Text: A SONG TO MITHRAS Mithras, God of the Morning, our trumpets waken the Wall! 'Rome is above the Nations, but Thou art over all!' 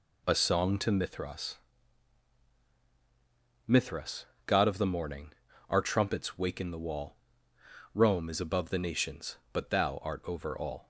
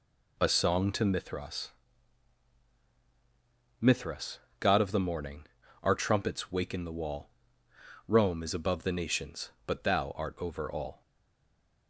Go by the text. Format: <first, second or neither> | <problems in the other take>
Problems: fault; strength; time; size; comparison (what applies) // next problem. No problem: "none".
first | pauses between "MITHRAS" and "Mithras"; strong; at 1.7 s; 2.1 s long; strong in the first // stays silent after the last word; slight; from 11.0 s on; 0.8 s long